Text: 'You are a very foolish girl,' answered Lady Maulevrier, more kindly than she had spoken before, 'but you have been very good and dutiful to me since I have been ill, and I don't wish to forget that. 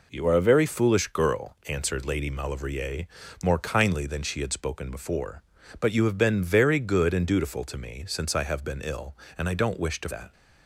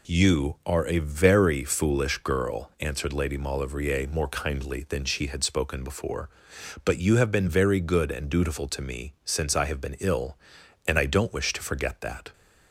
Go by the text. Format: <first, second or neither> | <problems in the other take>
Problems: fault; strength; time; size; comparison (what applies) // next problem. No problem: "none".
second | skips "forget"; at 10.0 s